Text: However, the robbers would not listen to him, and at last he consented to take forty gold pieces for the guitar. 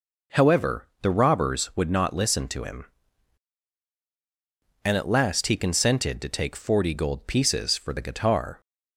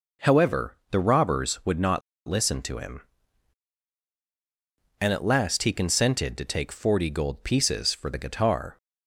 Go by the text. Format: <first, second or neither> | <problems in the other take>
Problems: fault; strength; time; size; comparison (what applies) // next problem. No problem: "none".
first | pauses between "not" and "listen"; slight; at 2.0 s; 0.27 s long